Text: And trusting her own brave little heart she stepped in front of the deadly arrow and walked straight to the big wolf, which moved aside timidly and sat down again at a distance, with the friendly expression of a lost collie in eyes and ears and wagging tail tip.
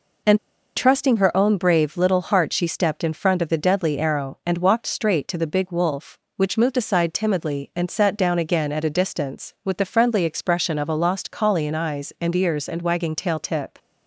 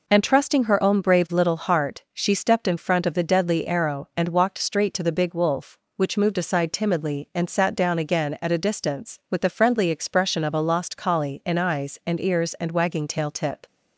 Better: second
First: pauses between "And" and "trusting"; at 0.3 s; 0.37 s long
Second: none

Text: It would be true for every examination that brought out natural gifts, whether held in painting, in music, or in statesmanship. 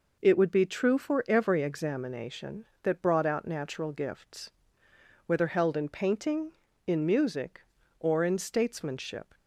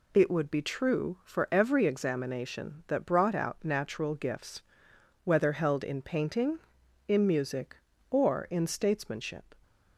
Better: neither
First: none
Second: none

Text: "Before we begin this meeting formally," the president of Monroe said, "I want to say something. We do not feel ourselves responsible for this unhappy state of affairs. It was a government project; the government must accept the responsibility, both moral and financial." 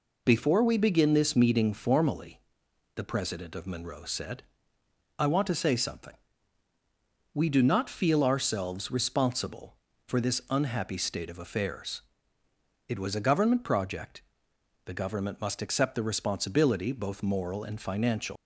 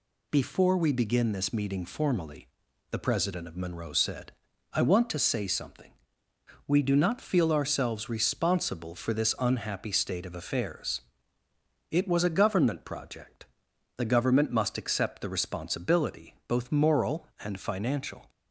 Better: second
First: leaves "financial" unfinished; at 18.3 s; 110 ms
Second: none

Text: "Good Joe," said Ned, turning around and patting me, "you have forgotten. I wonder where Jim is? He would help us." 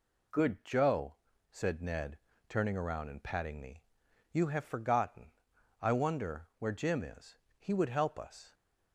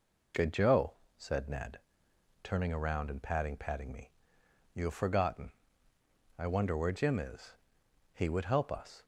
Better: first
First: none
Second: says "patting" twice; at 3.5 s

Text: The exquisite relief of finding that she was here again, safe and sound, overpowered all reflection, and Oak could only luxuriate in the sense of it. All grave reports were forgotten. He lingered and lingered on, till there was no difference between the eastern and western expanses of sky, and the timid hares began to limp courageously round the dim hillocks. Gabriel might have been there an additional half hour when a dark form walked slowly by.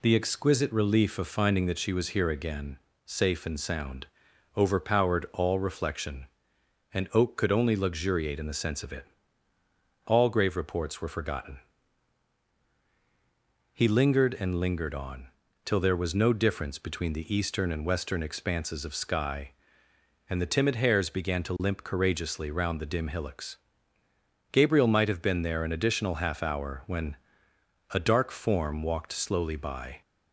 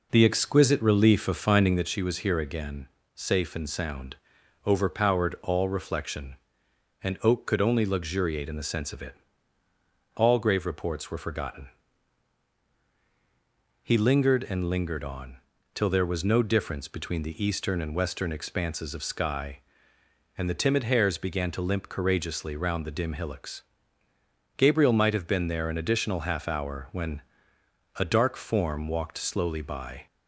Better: first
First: pauses between "when" and "a"; noticeable; at 27.1 s; 0.76 s long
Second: starts louder than the rest; noticeable; until 2.0 s; 4.5 dB // pauses between "when" and "a"; noticeable; at 27.2 s; 0.76 s long

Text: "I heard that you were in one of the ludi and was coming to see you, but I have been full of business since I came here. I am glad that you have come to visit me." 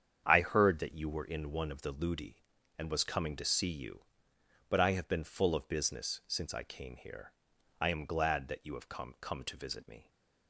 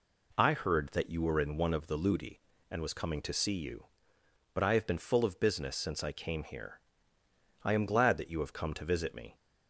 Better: second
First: starts louder than the rest; strong; until 1.2 s; 8 dB // says "come" twice; at 9.2 s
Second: none

